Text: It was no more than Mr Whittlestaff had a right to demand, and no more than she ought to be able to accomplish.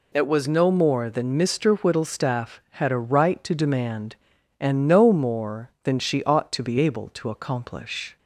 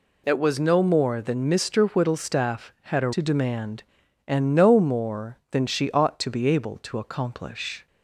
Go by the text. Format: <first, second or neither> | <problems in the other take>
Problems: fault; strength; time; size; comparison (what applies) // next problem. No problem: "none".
first | skips "right"; at 3.1 s